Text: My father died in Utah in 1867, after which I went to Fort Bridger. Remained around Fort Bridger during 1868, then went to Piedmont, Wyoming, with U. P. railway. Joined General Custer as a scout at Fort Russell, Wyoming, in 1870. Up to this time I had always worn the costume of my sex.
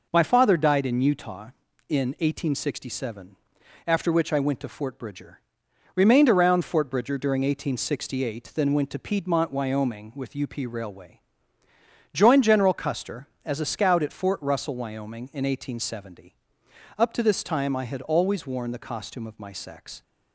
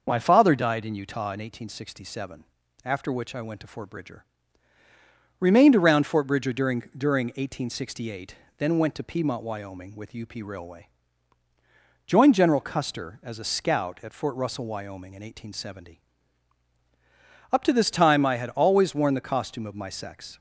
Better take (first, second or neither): first